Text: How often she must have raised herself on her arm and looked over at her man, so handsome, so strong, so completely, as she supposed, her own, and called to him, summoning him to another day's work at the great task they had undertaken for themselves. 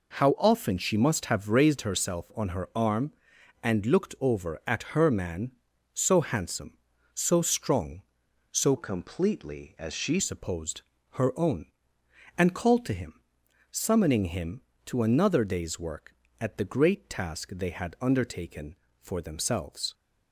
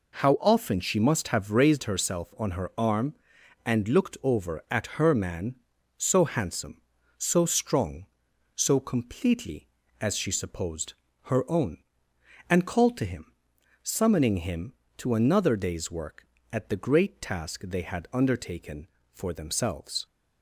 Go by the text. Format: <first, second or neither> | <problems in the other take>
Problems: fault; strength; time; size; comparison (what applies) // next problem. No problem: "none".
second | changes voice from "completely" to "she"; from 8.7 to 10.2 s; 1.5 s long